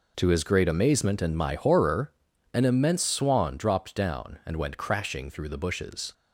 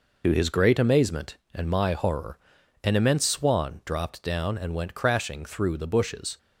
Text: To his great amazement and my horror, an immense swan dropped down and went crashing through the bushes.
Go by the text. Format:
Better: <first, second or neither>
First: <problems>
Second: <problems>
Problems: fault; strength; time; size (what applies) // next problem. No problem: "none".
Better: first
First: none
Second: loses the start of "To"; at 0.2 s; 50 ms